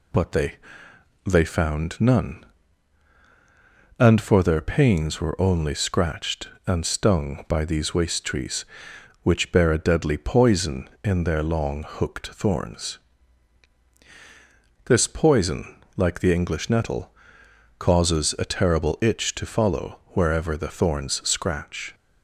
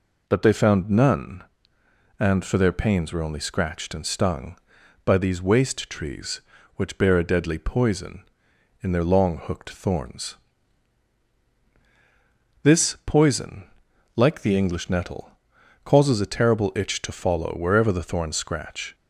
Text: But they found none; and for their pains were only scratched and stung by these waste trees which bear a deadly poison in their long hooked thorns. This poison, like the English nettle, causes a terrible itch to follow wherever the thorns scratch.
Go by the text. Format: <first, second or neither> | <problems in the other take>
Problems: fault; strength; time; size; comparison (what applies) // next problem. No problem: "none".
second | says "they" twice; at 1.2 s